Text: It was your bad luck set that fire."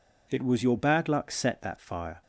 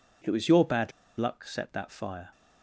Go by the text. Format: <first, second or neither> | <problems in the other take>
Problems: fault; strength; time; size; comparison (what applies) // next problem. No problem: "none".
first | pauses between "bad" and "luck"; slight; at 0.9 s; 0.27 s long